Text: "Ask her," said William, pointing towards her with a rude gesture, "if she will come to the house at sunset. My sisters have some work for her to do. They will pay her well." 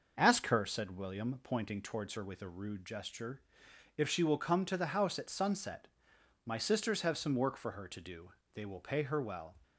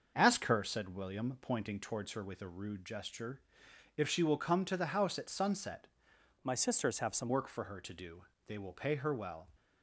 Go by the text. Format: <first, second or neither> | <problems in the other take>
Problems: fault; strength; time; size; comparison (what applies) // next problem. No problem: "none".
first | starts louder than the rest; until 1.1 s; 6 dB // changes voice from "My" to "some"; from 6.4 to 7.3 s; 0.9 s long